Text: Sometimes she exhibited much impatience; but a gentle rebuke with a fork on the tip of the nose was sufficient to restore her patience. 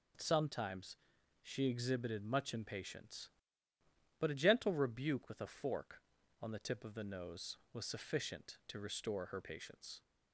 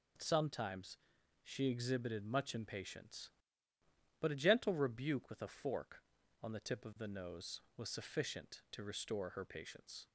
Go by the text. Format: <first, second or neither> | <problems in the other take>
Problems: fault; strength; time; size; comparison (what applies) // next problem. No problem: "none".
neither | pauses between "Sometimes" and "she"; noticeable; the same in both